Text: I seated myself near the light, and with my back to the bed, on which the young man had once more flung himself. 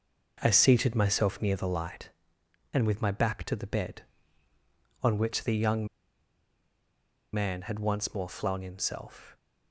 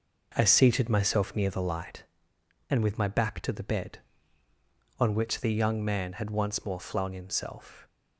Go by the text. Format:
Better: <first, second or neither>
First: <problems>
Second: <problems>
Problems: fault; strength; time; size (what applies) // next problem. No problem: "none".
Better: second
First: pauses between "young" and "man"; strong; at 5.8 s; 1.4 s long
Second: none